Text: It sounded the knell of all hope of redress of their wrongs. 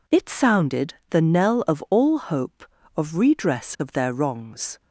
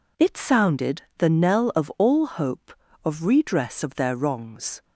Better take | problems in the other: neither | pauses between "sounded" and "the"; slight; the same in both

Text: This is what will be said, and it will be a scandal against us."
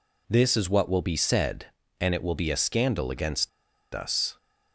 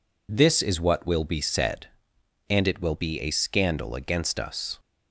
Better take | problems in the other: second | pauses between "against" and "us"; at 3.4 s; 0.45 s long

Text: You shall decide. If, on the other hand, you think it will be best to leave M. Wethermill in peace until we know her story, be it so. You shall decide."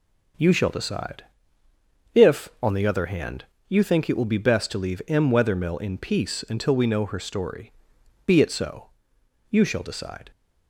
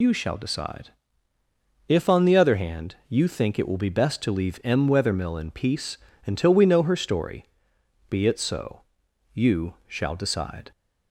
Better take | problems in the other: first | loses the start of "You"; at 0.0 s; 95 ms // pauses between "peace" and "until"; slight; at 5.9 s; 0.28 s long

